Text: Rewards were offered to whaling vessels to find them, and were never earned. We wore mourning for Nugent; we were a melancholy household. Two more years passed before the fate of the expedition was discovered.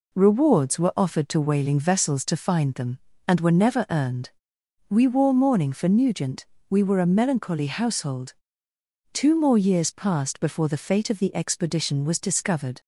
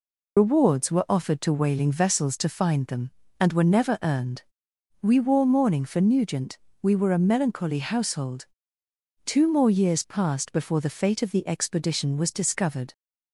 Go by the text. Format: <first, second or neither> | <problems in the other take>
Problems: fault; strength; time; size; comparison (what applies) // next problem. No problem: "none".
first | loses the start of "Rewards"; at 0.3 s; 105 ms